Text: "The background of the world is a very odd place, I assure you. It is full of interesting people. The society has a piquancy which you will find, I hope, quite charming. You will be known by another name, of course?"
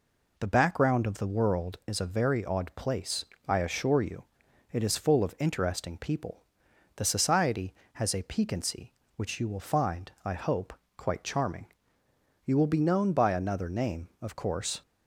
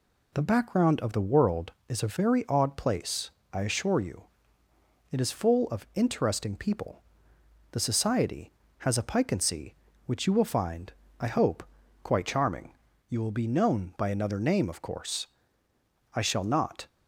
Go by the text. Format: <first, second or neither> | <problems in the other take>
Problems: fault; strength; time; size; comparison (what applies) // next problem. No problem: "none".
first | goes on to say "I shall not"; noticeable; from 16.1 s on; 0.72 s long